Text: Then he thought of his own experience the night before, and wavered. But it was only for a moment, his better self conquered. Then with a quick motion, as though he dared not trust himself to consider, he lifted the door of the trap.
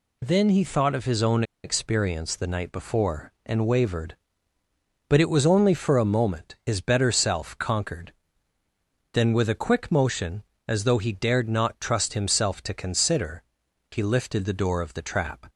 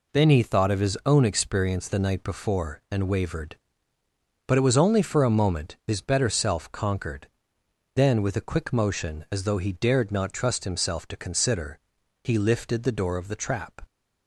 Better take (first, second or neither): second